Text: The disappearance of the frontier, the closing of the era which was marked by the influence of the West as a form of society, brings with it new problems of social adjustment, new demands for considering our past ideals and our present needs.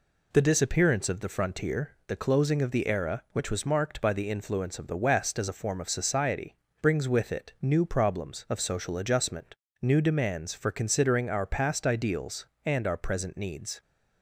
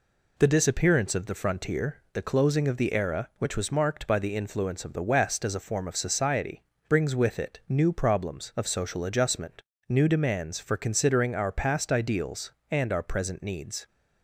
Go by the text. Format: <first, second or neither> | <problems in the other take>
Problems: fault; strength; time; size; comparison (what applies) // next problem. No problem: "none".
neither | none